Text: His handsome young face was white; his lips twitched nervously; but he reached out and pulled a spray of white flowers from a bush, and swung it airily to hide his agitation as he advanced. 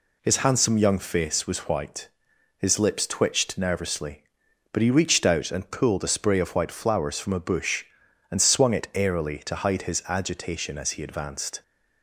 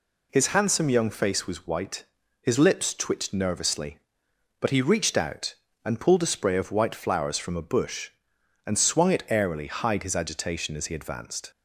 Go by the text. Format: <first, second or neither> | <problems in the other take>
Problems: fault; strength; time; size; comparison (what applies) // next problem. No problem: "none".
first | skips "to"; at 9.6 s